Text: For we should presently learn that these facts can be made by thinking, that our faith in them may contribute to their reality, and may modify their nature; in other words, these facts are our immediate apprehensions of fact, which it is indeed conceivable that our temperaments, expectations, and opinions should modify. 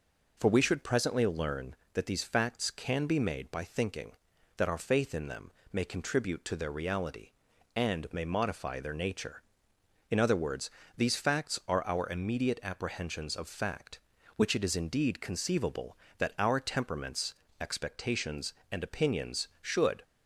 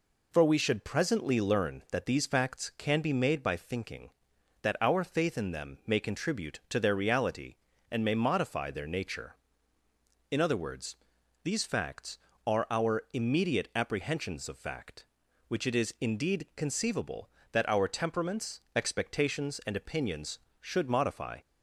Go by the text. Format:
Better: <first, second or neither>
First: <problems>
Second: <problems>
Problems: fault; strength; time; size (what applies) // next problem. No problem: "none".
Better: second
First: pauses between "them" and "may"; slight; at 5.5 s; 0.20 s long // stops before "modify"; at 20.0 s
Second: none